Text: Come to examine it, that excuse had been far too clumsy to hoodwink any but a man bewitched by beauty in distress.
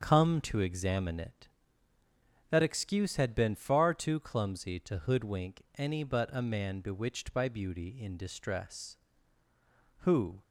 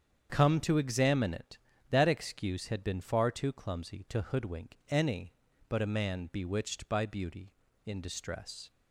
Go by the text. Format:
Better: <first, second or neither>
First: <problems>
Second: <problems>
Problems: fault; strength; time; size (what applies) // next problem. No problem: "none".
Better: second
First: starts louder than the rest; until 1.0 s; 7 dB // pauses between "hoodwink" and "any"; slight; at 5.6 s; 0.16 s long // goes on to say "Who"; slight; from 9.9 s on; 0.42 s long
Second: starts louder than the rest; strong; until 1.3 s; 8 dB